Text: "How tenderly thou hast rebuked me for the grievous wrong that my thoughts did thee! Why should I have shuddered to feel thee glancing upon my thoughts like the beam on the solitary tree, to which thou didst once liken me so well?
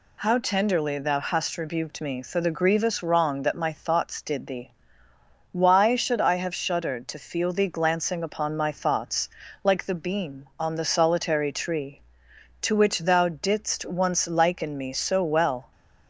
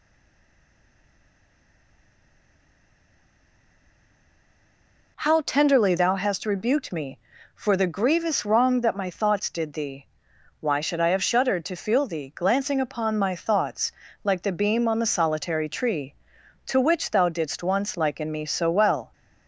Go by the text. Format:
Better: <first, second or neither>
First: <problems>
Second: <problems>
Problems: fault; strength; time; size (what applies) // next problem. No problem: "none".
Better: first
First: pauses between "thoughts" and "like"; slight; at 9.2 s; 0.34 s long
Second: stays silent before the first word; strong; until 5.1 s; 5.1 s long // pauses between "thoughts" and "like"; slight; at 13.9 s; 0.32 s long